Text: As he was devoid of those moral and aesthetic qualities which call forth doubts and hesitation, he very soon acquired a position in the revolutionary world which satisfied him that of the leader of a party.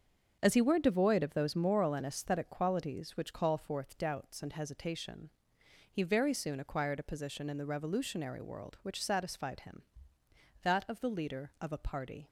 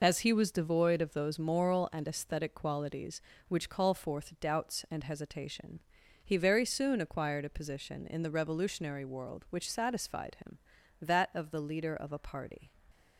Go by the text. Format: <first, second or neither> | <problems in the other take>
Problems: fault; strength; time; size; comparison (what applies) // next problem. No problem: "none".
second | starts louder than the rest; until 1.4 s; 7 dB // says "were" for "was"; at 0.6 s